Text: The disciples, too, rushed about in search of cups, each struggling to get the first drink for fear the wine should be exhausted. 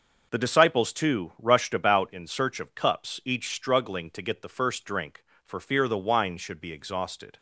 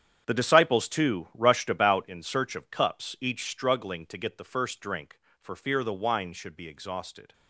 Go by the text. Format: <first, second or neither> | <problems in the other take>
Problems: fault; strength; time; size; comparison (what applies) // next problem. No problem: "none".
first | gets quieter; strong; throughout; 13 dB